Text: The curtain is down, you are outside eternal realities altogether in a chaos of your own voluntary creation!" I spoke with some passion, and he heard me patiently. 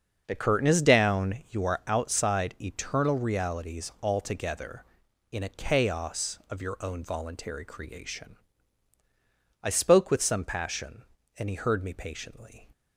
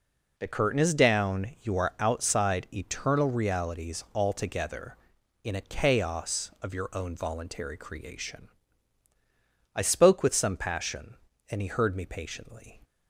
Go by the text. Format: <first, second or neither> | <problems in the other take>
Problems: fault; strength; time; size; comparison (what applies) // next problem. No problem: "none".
second | starts louder than the rest; until 1.6 s; 6.5 dB